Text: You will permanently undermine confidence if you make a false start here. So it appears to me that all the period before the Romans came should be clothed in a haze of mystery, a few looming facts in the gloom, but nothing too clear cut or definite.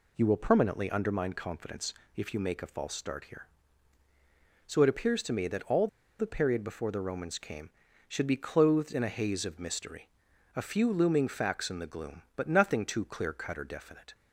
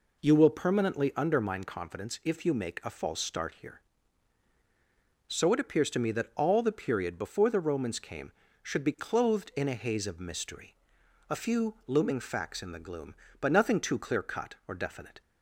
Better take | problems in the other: second | pauses between "confidence" and "if"; slight; at 1.9 s; 0.22 s long // pauses between "all" and "the"; slight; at 5.8 s; 0.32 s long

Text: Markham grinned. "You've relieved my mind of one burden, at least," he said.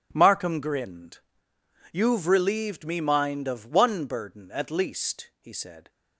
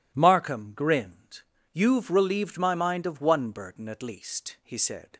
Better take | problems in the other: second | says "me" for "my"; at 2.8 s

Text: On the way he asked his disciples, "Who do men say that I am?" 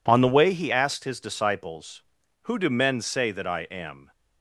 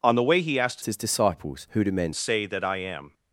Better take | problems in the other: first | changes voice from "his" to "men"; from 0.8 to 2.1 s; 1.3 s long

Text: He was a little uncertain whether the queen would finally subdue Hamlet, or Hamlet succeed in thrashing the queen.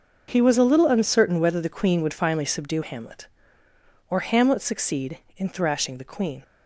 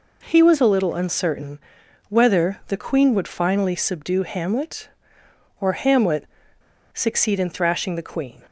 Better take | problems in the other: first | pauses between "uncertain" and "whether"; noticeable; at 1.5 s; 0.50 s long // pauses between "Hamlet" and "succeed"; noticeable; at 6.2 s; 0.67 s long

